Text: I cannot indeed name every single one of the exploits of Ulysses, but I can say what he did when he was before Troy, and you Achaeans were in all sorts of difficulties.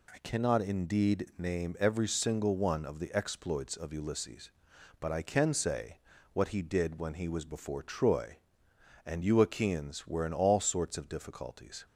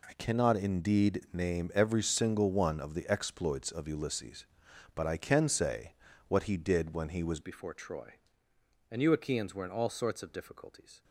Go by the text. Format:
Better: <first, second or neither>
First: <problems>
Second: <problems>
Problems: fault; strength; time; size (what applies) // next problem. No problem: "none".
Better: first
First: pauses between "say" and "what"; slight; at 5.9 s; 0.36 s long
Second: pauses between "say" and "what"; slight; at 5.9 s; 0.36 s long // changes voice at "before"; from 7.4 s on; 3.6 s long